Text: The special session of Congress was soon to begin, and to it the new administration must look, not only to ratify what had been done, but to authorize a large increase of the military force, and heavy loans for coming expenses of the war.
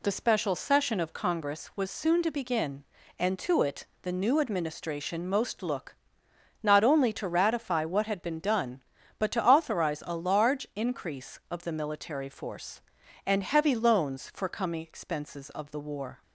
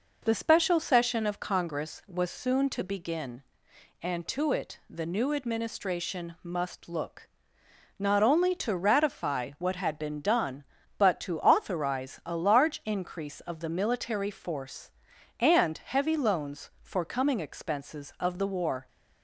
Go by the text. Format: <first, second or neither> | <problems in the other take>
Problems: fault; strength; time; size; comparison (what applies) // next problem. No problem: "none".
second | pauses between "it" and "the"; slight; at 3.8 s; 0.16 s long // says "most" for "must"; at 5.2 s